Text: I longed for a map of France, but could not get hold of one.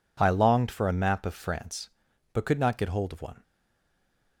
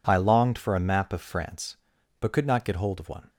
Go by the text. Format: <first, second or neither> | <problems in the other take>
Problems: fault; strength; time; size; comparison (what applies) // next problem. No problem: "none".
second | stays silent after the last word; from 3.4 s on; 1.0 s long